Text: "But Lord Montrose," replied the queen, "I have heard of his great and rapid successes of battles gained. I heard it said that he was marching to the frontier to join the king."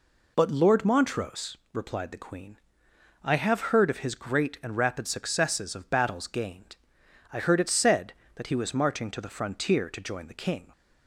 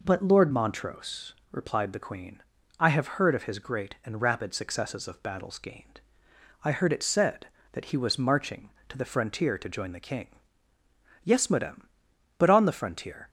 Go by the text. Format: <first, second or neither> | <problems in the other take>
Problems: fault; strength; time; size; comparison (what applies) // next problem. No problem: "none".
first | goes on to say "Yes madame but on the frontier"; strong; from 11.2 s on; 2.0 s long